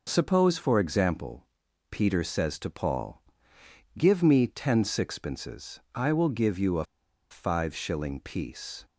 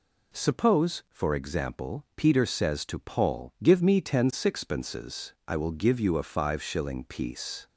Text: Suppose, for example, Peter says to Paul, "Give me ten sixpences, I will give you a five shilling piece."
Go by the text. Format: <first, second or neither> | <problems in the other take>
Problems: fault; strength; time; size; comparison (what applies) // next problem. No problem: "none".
second | pauses between "a" and "five"; at 6.8 s; 0.45 s long